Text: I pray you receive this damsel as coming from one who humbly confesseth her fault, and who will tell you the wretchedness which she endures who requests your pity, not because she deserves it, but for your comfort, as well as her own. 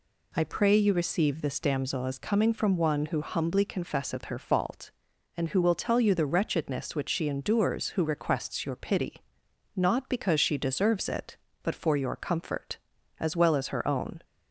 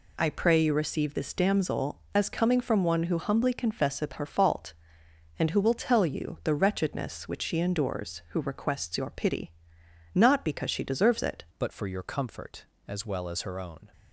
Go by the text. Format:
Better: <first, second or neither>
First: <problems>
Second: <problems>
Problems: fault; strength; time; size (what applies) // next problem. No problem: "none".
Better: first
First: none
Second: changes voice at "but"; from 11.5 s on; 2.4 s long